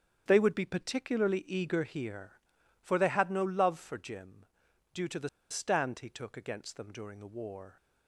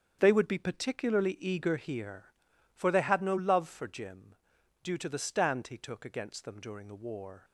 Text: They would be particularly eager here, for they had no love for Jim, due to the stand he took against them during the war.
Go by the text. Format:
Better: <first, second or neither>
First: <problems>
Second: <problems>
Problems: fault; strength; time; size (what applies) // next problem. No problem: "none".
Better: second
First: starts louder than the rest; strong; until 1.2 s; 7.5 dB // pauses between "the" and "stand"; slight; at 5.2 s; 0.21 s long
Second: starts louder than the rest; strong; until 1.2 s; 7.5 dB